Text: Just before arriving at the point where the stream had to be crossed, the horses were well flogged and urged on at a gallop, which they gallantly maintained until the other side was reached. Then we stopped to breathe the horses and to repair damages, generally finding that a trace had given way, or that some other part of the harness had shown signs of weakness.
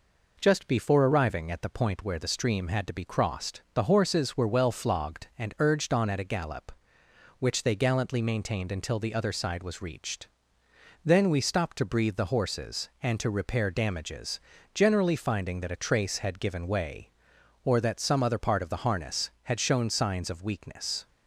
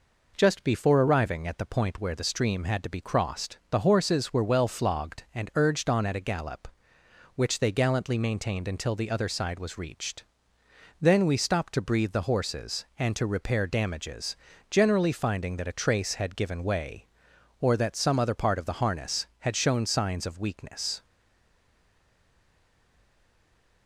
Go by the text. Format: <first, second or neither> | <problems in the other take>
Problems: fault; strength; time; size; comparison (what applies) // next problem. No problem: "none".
first | stays silent after the last word; strong; from 21.0 s on; 2.8 s long